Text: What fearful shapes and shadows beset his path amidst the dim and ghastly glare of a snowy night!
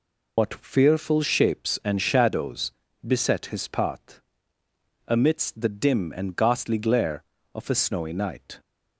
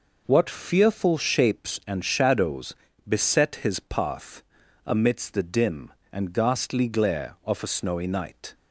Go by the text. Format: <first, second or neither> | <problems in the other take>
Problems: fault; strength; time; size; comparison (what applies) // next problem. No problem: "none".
second | loses the start of "What"; at 0.3 s; 160 ms // pauses between "shadows" and "beset"; slight; at 2.7 s; 0.34 s long; slight in the second // pauses between "path" and "amidst"; noticeable; at 4.1 s; 0.88 s long; also in the second